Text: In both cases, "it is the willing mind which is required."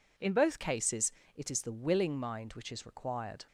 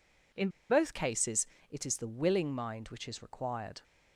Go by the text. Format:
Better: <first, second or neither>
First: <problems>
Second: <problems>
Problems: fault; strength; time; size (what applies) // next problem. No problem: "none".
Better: first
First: none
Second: pauses between "In" and "both"; slight; at 0.4 s; 0.21 s long